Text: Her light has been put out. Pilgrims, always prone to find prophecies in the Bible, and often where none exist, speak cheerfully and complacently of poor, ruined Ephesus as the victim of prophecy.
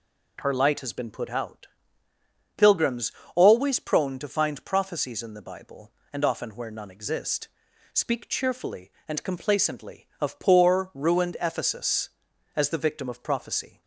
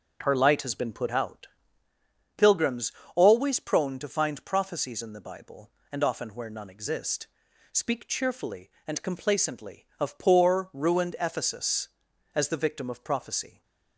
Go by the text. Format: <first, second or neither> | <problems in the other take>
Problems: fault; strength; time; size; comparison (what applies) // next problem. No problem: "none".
first | starts louder than the rest; noticeable; until 1.9 s; 6 dB